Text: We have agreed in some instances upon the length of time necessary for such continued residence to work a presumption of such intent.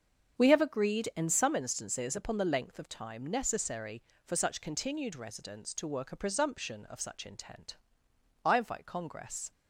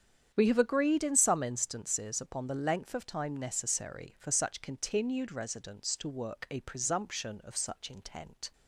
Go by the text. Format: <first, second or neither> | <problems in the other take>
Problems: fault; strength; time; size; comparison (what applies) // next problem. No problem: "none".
second | starts louder than the rest; strong; until 1.4 s; 7.5 dB; strong in the second // goes on to say "I invite Congress"; noticeable; from 8.4 s on; 1.0 s long